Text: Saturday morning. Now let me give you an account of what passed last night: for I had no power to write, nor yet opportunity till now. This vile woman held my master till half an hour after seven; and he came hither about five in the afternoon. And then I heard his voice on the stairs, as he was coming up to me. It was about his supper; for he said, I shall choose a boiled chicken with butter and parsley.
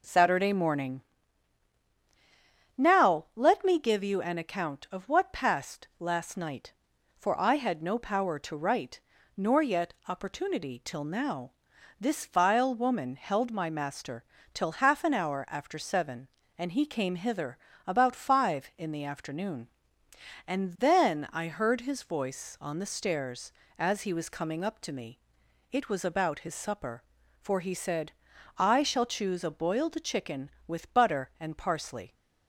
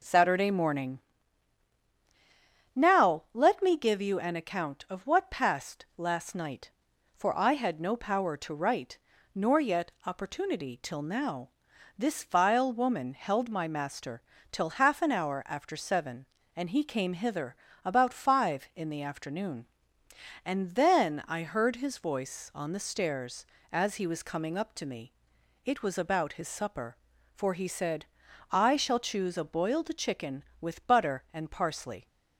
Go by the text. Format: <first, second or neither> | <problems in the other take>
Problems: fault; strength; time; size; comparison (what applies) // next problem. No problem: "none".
neither | pauses between "master" and "till"; slight; the same in both // pauses between "hither" and "about"; slight; the same in both